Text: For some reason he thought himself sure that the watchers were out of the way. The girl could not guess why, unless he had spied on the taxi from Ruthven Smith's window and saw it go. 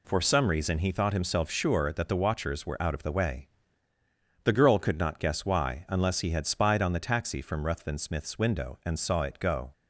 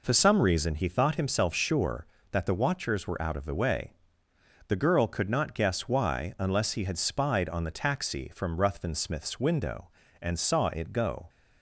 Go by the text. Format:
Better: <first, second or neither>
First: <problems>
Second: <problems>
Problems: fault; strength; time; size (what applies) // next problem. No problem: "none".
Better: neither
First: none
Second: none